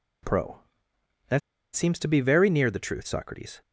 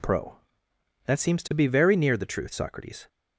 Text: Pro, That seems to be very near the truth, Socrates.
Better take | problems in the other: second | pauses between "That" and "seems"; slight; at 1.4 s; 0.35 s long

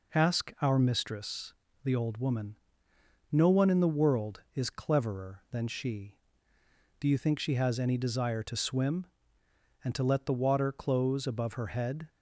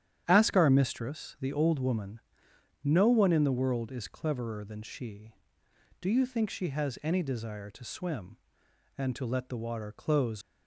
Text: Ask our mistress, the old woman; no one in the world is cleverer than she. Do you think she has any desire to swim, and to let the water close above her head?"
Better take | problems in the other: first | starts louder than the rest; strong; until 1.2 s; 9.5 dB // stops before "above her head"; at 10.4 s

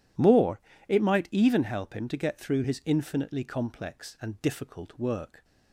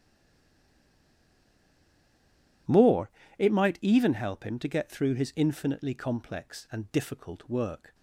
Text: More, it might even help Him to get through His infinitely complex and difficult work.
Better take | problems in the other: first | stays silent before the first word; strong; until 2.6 s; 2.6 s long

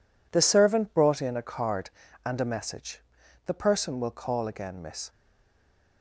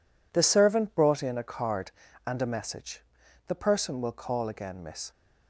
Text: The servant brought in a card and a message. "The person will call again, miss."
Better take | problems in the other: second | stays silent after the last word; slight; from 5.1 s on; 0.9 s long

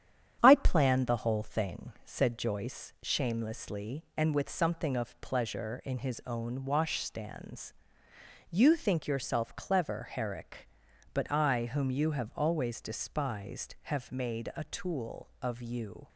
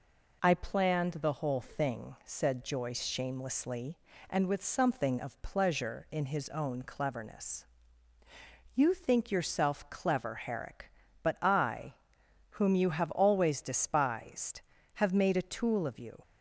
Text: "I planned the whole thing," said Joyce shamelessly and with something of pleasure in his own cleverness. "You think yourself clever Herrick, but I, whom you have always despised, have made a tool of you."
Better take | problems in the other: second | starts louder than the rest; strong; until 1.4 s; 9.5 dB // says "washstands" for "cleverness"; at 6.6 s

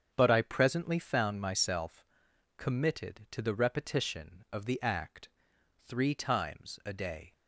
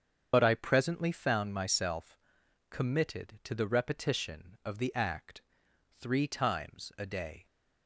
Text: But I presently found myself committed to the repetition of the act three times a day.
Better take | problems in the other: first | loses the start of "But"; at 0.3 s; 65 ms // starts louder than the rest; strong; until 1.3 s; 7.5 dB; strong in the first // pauses between "myself" and "committed"; noticeable; at 2.1 s; 0.54 s long; noticeable in the first // pauses between "act" and "three"; noticeable; at 5.4 s; 0.58 s long; noticeable in the first

